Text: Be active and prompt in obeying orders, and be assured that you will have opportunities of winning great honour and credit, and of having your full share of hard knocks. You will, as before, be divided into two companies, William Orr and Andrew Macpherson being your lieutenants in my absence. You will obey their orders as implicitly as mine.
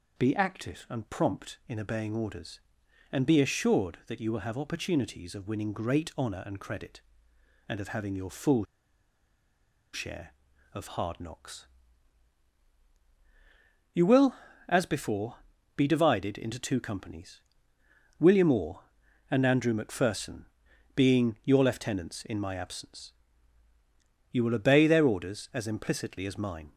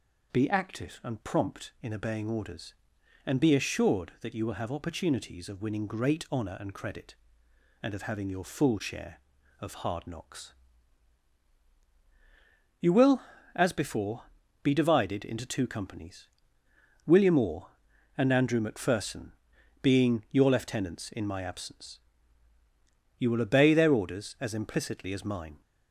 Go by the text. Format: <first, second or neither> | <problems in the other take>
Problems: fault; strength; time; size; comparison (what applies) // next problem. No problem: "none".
second | pauses between "full" and "share"; strong; at 8.6 s; 1.2 s long // pauses between "Macpherson" and "being"; noticeable; at 20.4 s; 0.50 s long; noticeable in the second